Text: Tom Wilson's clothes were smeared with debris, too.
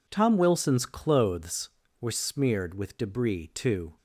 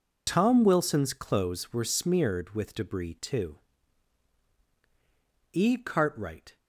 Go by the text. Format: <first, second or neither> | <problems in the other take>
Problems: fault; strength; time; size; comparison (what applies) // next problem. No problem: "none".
first | goes on to say "E Cartwright"; noticeable; from 5.5 s on; 1.0 s long